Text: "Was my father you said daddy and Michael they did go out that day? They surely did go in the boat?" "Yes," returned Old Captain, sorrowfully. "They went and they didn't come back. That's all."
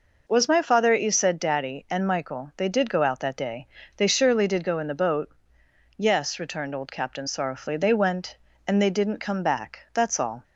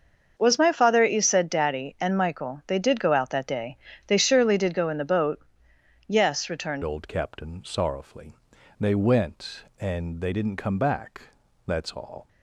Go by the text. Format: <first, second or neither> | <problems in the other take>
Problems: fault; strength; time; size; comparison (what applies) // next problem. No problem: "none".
first | starts louder than the rest; until 1.3 s; 6.5 dB // changes voice at "Old"; from 6.8 s on; 5.4 s long